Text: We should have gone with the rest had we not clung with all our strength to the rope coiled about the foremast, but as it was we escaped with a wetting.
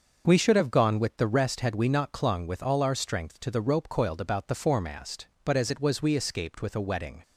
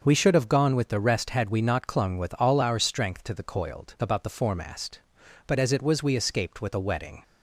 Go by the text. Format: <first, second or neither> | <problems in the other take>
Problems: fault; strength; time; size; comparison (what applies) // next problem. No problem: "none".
first | starts louder than the rest; until 1.0 s; 6.5 dB; also in the first // skips "rope"; at 3.4 s